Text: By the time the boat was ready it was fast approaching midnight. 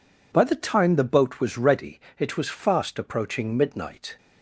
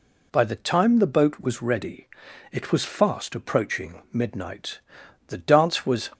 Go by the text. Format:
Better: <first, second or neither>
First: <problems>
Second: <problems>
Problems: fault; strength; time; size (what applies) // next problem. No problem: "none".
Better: first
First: pauses between "ready" and "it"; slight; at 2.0 s; 0.16 s long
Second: pauses between "ready" and "it"; noticeable; at 2.0 s; 0.46 s long // goes on to say "The dance was"; noticeable; from 5.2 s on; 0.84 s long